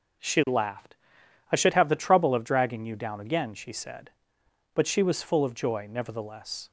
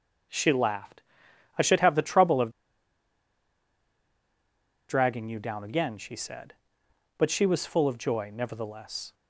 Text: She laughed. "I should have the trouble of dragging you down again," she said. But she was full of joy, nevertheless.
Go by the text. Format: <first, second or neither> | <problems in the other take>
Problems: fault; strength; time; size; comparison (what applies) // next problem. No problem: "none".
first | starts louder than the rest; until 1.8 s; 6 dB; noticeable in the first // pauses between "of" and "dragging"; strong; at 2.5 s; 2.3 s long